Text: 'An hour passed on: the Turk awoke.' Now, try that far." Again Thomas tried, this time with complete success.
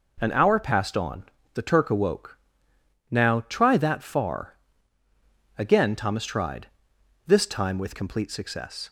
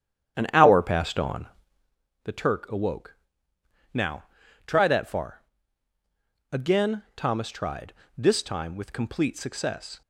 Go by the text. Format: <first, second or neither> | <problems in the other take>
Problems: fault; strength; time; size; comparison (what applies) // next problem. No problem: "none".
first | starts louder than the rest; strong; until 2.0 s; 9.5 dB